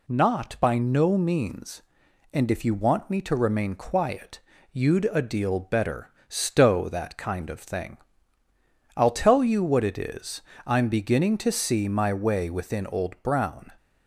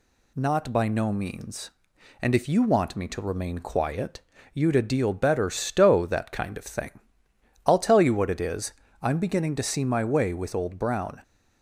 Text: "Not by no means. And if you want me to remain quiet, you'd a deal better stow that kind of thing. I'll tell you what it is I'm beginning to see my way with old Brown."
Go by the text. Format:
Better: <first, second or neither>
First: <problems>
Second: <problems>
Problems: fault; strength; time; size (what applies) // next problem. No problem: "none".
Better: second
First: pauses between "better" and "stow"; slight; at 6.1 s; 0.18 s long // pauses between "is" and "I'm"; slight; at 10.4 s; 0.26 s long // says "within" for "with"; at 12.5 s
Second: pauses between "is" and "I'm"; slight; at 8.7 s; 0.28 s long